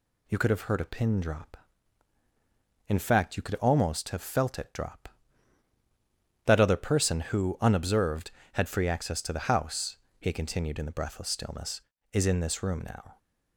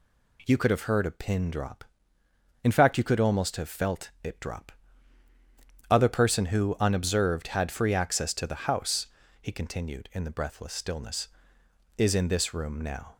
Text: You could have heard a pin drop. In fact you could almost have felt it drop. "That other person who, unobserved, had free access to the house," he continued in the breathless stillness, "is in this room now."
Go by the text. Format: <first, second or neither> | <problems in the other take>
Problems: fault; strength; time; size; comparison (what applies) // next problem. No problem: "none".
first | skips "That"; at 5.3 s